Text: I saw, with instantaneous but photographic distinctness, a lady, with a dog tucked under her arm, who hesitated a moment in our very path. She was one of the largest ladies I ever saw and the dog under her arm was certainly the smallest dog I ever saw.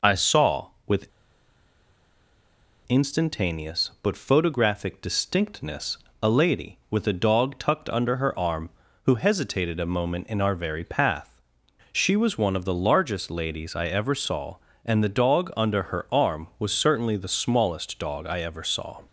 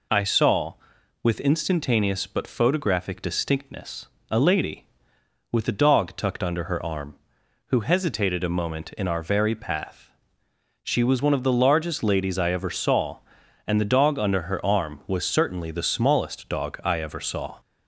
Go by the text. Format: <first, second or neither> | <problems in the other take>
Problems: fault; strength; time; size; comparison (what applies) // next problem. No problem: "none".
second | pauses between "with" and "instantaneous"; strong; at 1.0 s; 1.8 s long